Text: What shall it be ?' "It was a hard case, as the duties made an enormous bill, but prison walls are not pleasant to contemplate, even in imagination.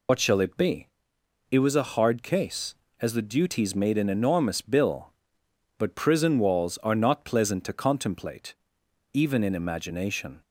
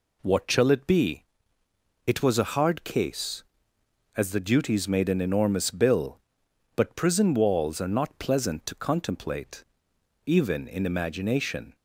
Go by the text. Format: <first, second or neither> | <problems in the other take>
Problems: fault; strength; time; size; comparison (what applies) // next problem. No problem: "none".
second | loses the start of "What"; at 0.0 s; 70 ms